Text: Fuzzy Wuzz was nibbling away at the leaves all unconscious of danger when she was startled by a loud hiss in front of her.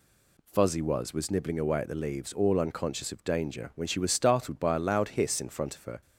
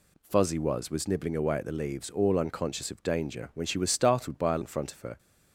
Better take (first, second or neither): first